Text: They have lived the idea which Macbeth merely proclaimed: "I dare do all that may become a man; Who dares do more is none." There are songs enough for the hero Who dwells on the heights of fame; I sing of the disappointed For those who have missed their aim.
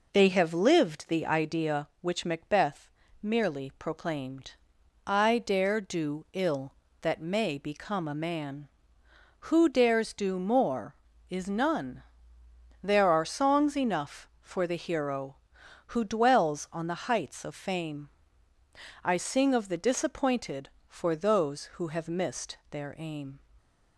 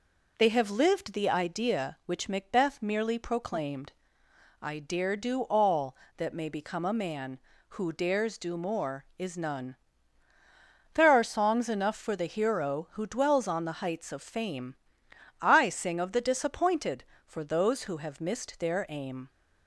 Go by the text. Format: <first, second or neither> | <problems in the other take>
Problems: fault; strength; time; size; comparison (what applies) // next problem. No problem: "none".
second | pauses between "Macbeth" and "merely"; slight; at 2.8 s; 0.32 s long // says "ill" for "all"; at 6.3 s